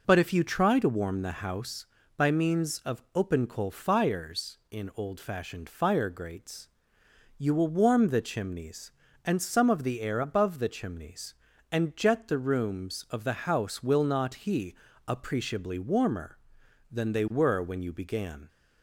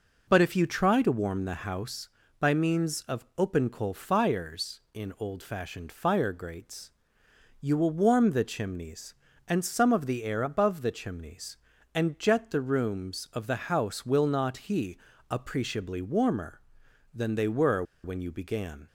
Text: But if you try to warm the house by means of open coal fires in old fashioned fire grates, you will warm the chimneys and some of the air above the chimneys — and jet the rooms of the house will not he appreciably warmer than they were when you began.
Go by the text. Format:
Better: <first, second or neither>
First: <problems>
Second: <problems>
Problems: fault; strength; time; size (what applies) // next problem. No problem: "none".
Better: first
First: pauses between "he" and "appreciably"; slight; at 14.7 s; 0.32 s long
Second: pauses between "he" and "appreciably"; slight; at 14.9 s; 0.32 s long // pauses between "were" and "when"; slight; at 17.8 s; 0.21 s long